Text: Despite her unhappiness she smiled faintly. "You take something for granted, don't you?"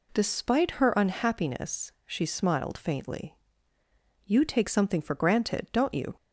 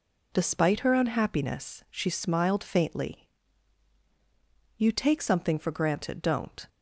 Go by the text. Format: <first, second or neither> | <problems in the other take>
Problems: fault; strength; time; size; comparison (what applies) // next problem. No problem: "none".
first | stops before "you"; at 6.6 s